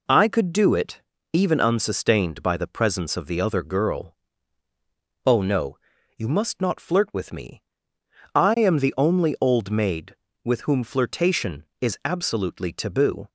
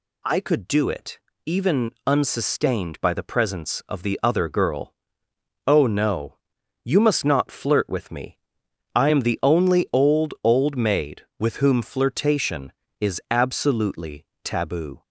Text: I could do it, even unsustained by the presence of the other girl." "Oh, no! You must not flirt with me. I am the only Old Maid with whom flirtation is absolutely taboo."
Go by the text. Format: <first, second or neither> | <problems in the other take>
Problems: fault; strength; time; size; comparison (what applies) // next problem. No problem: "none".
first | pauses between "even" and "unsustained"; slight; at 1.9 s; 0.16 s long // says "Old" twice; at 10.4 s // pauses between "absolutely" and "taboo"; slight; at 14.2 s; 0.18 s long